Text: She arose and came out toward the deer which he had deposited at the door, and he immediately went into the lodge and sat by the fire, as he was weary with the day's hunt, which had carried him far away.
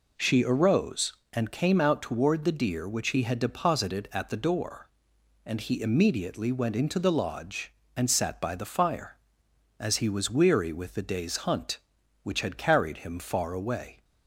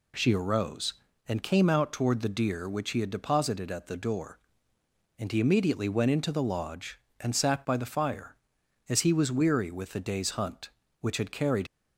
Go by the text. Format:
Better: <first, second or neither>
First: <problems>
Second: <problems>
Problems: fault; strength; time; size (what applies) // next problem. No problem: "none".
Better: first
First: none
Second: stops before "him far away"; at 11.6 s